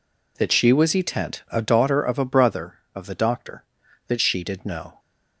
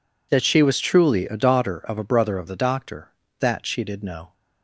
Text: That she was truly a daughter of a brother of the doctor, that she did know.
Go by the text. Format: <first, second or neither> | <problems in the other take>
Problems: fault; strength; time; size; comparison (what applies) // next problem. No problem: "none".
second | says "etent" for "truly"; at 0.9 s